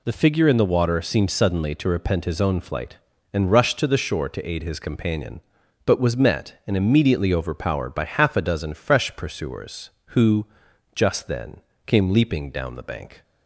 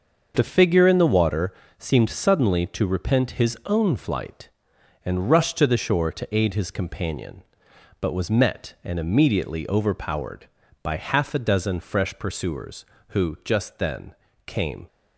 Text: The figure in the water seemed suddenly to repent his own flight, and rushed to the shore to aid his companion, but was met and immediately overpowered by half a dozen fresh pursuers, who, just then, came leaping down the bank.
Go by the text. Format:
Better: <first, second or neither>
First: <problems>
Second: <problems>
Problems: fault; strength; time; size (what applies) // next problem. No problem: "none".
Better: first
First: none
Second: starts louder than the rest; until 1.3 s; 6.5 dB // pauses between "water" and "seemed"; slight; at 1.5 s; 0.24 s long // stops before "leaping down the bank"; at 14.8 s